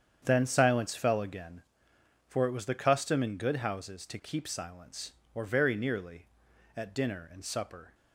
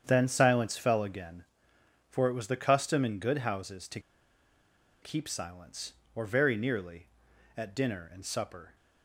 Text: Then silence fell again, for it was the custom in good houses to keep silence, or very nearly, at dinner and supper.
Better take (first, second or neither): first